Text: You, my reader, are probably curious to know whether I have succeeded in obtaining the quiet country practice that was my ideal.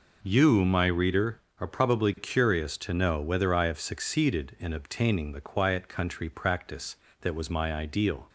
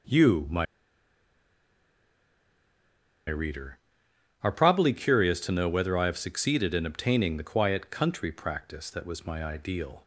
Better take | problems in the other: first | pauses between "my" and "reader"; strong; at 0.6 s; 2.6 s long

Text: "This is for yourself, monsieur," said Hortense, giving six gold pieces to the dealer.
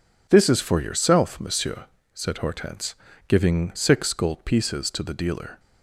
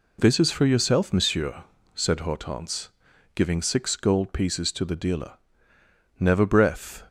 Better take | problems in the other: first | goes on to say "Never breath"; noticeable; from 6.1 s on; 0.86 s long

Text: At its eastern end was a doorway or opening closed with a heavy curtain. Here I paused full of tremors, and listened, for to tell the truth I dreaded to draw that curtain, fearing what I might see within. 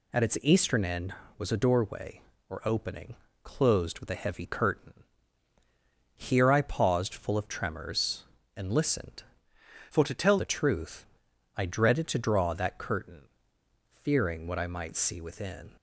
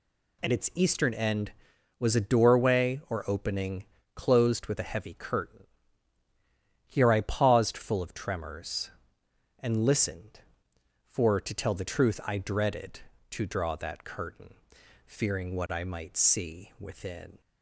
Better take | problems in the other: second | pauses between "opening" and "closed"; slight; at 3.1 s; 0.30 s long; slight in the second // changes voice from "for" to "tell"; from 9.8 to 10.3 s; 0.5 s long // pauses between "truth" and "I"; noticeable; at 11.0 s; 0.50 s long

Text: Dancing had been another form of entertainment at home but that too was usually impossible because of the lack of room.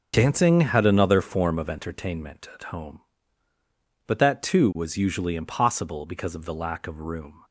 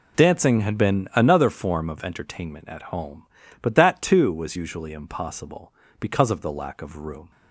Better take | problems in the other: second | starts louder than the rest; until 1.1 s; 7 dB // skips "been"; at 0.8 s

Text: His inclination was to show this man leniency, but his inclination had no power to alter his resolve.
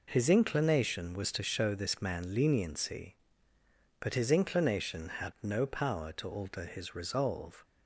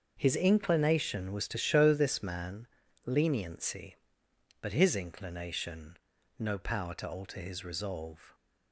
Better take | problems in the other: first | starts louder than the rest; until 1.1 s; 6.5 dB // pauses between "man" and "leniency"; at 2.6 s; 0.38 s long // skips "had"; at 6.1 s

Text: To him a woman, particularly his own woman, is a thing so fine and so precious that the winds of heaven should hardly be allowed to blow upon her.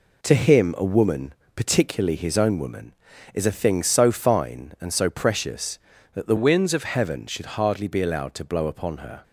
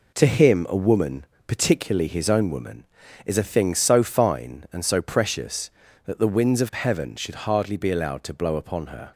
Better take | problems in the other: second | changes voice from "winds" to "of"; from 6.3 to 6.8 s; 0.5 s long

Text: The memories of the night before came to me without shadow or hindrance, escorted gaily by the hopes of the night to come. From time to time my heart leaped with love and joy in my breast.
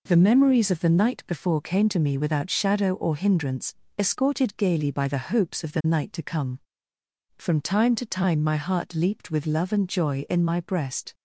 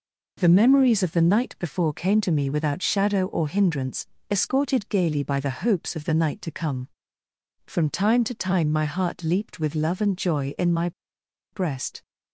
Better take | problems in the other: first | pauses between "my" and "breast"; noticeable; at 10.9 s; 0.62 s long

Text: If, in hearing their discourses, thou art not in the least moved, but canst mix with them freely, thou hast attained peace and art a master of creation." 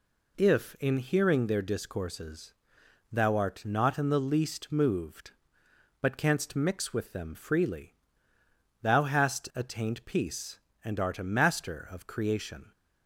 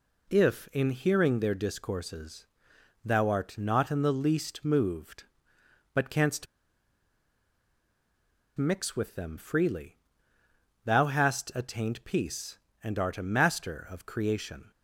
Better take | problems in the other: first | pauses between "canst" and "mix"; strong; at 6.4 s; 2.1 s long

